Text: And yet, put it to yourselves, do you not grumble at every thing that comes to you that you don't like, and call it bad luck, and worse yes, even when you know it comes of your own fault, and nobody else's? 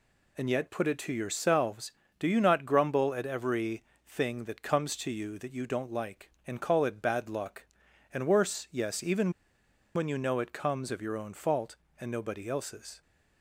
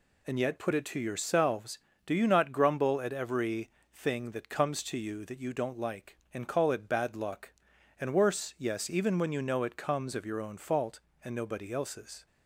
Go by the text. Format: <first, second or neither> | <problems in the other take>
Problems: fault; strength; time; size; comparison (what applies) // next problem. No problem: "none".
second | pauses between "every" and "thing"; slight; at 3.8 s; 0.24 s long; slight in the second // pauses between "even" and "when"; noticeable; at 9.3 s; 0.64 s long